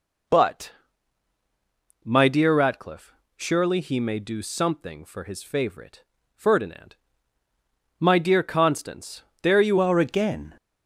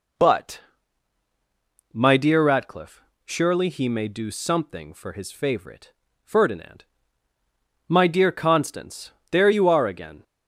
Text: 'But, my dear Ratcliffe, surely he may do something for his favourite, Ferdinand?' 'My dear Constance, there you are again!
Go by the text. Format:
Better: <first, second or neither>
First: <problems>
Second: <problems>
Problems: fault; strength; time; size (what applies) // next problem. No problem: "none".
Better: second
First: changes voice at "are"; from 9.8 s on; 0.7 s long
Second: none